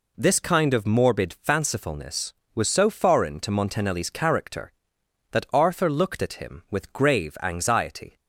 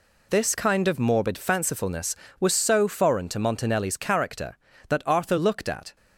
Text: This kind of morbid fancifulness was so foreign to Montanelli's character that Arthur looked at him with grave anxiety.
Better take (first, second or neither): first